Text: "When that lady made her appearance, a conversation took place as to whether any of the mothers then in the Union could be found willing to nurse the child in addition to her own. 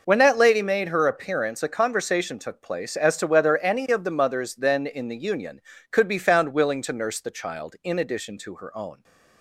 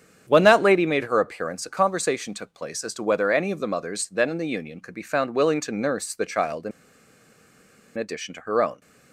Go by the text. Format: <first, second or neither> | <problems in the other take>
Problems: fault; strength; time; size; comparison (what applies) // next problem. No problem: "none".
first | starts louder than the rest; strong; until 1.2 s; 8.5 dB // pauses between "in" and "addition"; strong; at 6.7 s; 1.2 s long